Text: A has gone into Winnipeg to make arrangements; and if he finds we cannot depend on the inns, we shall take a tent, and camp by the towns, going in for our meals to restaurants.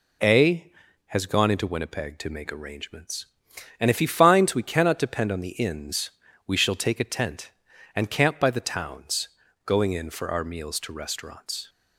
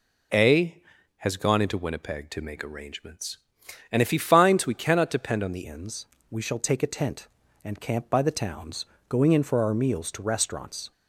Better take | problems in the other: first | changes voice at "inns"; from 5.6 s on; 5.3 s long

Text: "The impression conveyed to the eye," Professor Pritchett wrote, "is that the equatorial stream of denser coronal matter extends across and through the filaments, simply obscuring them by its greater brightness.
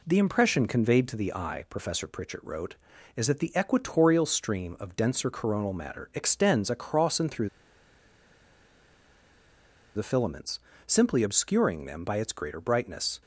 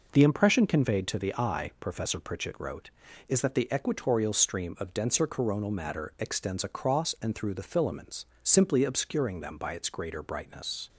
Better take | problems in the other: second | pauses between "through" and "the"; strong; at 7.4 s; 2.4 s long

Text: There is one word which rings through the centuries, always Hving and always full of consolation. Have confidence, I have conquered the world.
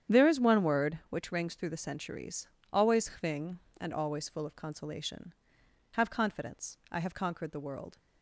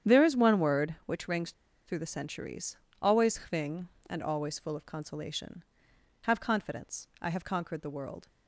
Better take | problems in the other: first | starts louder than the rest; strong; until 1.1 s; 9 dB; strong in the first // pauses between "rings" and "through"; slight; at 1.5 s; 0.34 s long

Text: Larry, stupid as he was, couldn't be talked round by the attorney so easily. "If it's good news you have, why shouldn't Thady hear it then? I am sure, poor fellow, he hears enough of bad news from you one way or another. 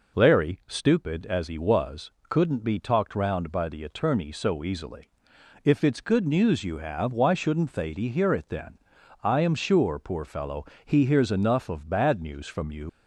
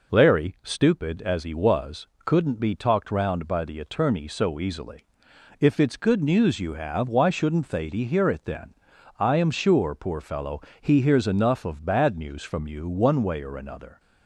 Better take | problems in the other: second | stops before "one way or another"; at 12.8 s

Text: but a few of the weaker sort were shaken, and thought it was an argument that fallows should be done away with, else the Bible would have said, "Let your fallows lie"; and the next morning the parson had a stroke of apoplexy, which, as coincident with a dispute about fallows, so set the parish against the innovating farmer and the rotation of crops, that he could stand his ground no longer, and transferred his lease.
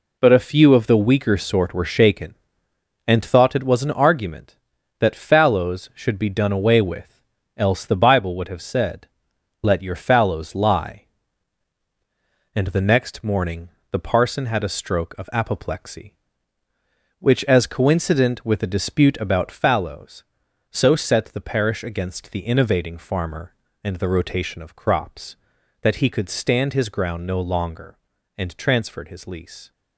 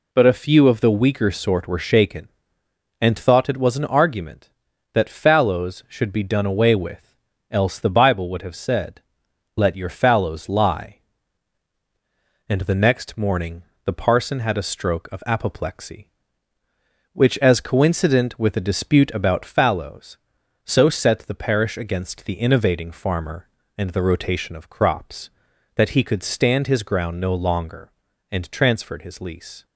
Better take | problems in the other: second | gets quieter; strong; throughout; 7.5 dB // pauses between "morning" and "the"; slight; at 13.6 s; 0.22 s long; slight in the second

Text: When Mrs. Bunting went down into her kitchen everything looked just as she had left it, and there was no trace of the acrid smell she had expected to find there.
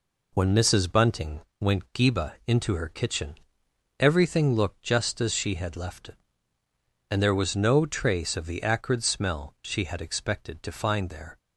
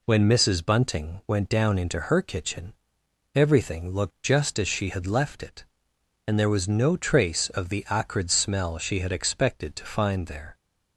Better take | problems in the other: second | pauses between "Bunting" and "went"; slight; at 1.4 s; 0.18 s long // says "geba" for "down"; at 1.9 s // pauses between "kitchen" and "everything"; noticeable; at 3.3 s; 0.64 s long; noticeable in the second

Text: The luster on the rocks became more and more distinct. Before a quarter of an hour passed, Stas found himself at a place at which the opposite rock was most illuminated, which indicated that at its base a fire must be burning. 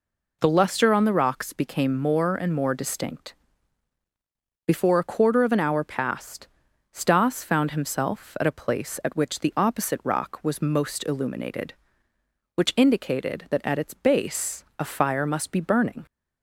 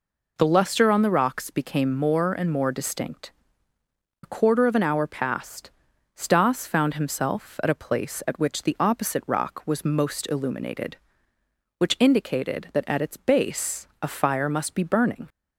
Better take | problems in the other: first | skips "Before"; at 3.7 s // pauses between "base" and "a"; slight; at 13.8 s; 0.16 s long; slight in the first

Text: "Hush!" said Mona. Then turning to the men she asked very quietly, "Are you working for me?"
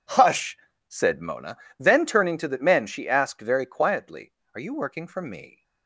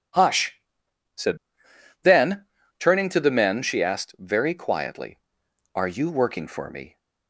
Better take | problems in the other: first | skips "Mona"; at 1.7 s // pauses between "Then" and "turning"; slight; at 2.4 s; 0.32 s long

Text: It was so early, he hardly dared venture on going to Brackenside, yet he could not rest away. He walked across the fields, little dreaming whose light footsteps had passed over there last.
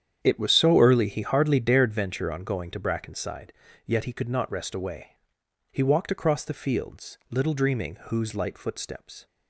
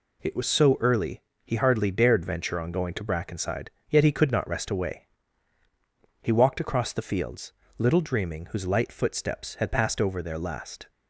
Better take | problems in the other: second | starts louder than the rest; strong; until 1.2 s; 9 dB // stops before "had passed over there last"; at 9.2 s

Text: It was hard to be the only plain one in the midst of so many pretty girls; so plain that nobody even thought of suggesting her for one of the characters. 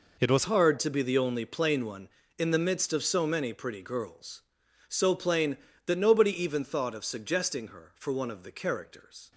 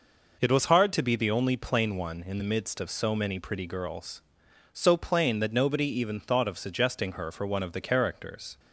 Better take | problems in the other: second | changes voice at "hard"; from 0.4 s on; 8.9 s long

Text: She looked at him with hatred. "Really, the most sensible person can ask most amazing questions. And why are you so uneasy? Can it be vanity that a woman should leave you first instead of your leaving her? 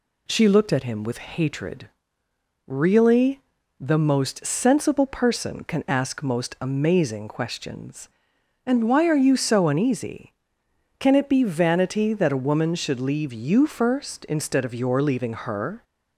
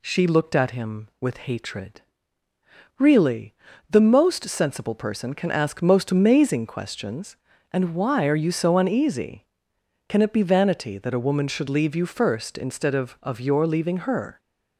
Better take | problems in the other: first | says "of" twice; at 13.2 s

